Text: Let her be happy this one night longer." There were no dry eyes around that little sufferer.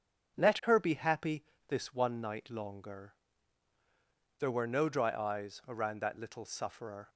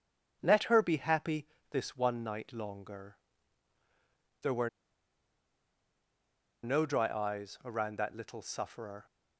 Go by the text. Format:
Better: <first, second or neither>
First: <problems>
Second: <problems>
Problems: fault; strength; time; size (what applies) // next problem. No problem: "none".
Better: first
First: starts louder than the rest; strong; until 1.4 s; 7.5 dB // pauses between "happy" and "this"; slight; at 1.4 s; 0.26 s long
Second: starts louder than the rest; strong; until 1.4 s; 7.5 dB // pauses between "happy" and "this"; slight; at 1.4 s; 0.26 s long // pauses between "were" and "no"; strong; at 4.6 s; 1.9 s long